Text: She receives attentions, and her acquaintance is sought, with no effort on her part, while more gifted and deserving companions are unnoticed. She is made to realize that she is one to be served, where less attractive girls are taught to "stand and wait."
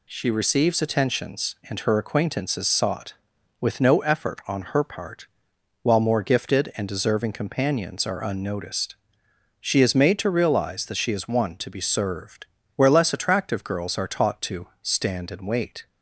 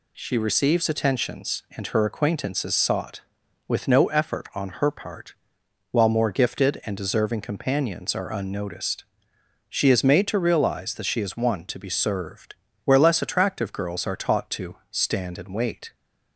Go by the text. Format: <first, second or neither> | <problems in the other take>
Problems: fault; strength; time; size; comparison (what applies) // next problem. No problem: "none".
neither | none